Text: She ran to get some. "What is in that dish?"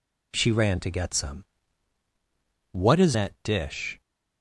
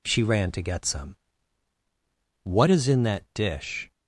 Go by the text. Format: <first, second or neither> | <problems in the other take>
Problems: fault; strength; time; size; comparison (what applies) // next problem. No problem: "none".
second | skips "in"; at 3.1 s